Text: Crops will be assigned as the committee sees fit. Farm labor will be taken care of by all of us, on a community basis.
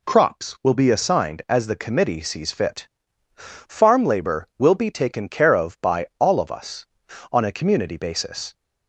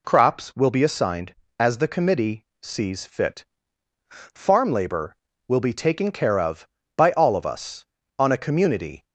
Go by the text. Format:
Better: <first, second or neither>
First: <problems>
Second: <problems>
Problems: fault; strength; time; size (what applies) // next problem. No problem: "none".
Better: first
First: none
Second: pauses between "committee" and "sees"; slight; at 2.4 s; 0.16 s long // stops before "basis"; at 9.0 s